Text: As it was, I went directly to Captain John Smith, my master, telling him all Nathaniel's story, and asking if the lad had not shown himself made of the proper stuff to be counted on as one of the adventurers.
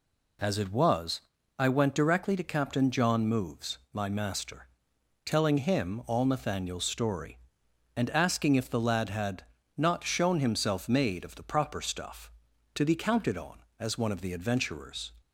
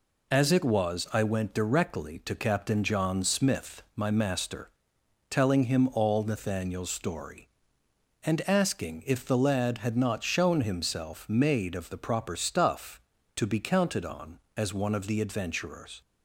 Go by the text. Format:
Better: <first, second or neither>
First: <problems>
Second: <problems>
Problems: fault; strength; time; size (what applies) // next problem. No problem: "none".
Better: second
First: says "Moves" for "Smith"; at 3.2 s // pauses between "had" and "not"; slight; at 9.4 s; 0.32 s long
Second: none